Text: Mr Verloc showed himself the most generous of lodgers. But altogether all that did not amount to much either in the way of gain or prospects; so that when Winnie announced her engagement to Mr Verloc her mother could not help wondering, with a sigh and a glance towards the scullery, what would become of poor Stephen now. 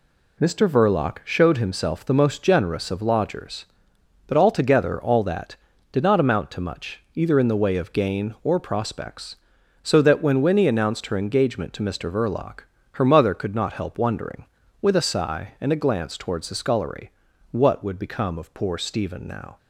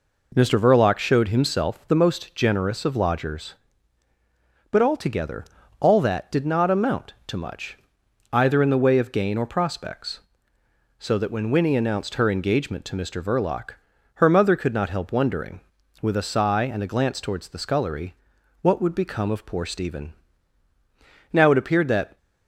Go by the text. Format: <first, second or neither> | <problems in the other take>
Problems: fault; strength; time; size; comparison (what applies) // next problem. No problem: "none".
first | pauses between "altogether" and "all"; slight; at 5.4 s; 0.34 s long // pauses between "much" and "either"; noticeable; at 7.7 s; 0.54 s long; slight in the first // pauses between "Verloc" and "her"; at 13.7 s; 0.40 s long; slight in the first // pauses between "Stephen" and "now"; at 20.1 s; 1.1 s long // goes on to say "It appeared that"; noticeable; from 21.5 s on; 0.66 s long